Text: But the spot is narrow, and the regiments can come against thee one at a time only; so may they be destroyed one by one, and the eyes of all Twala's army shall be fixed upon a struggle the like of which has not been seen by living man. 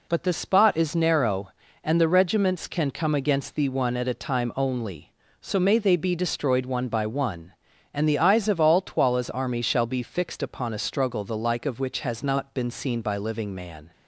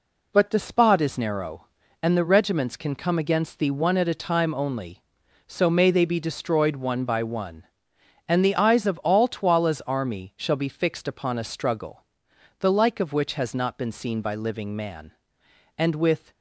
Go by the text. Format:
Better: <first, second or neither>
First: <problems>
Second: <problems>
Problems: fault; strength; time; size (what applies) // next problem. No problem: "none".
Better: first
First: none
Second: pauses between "struggle" and "the"; noticeable; at 12.0 s; 0.56 s long // goes on to say "And with"; from 15.7 s on; 0.54 s long